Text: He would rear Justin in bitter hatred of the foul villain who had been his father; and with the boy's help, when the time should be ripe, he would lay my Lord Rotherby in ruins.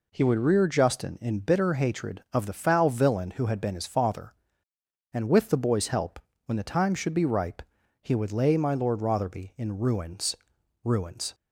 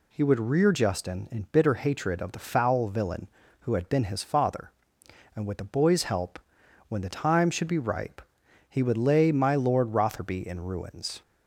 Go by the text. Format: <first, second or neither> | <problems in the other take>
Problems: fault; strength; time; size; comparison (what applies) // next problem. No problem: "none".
second | says "ruins" twice; at 10.8 s